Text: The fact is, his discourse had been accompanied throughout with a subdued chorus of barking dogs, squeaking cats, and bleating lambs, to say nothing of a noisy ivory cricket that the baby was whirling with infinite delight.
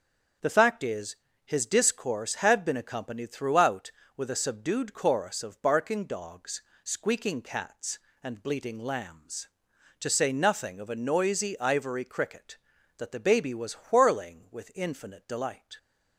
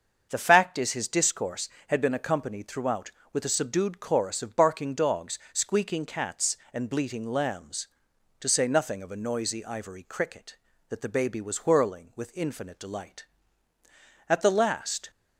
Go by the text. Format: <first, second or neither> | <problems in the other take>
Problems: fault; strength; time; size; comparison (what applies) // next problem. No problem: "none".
first | starts louder than the rest; until 1.3 s; 6.5 dB; also in the first // goes on to say "At the last"; noticeable; from 14.2 s on; 0.82 s long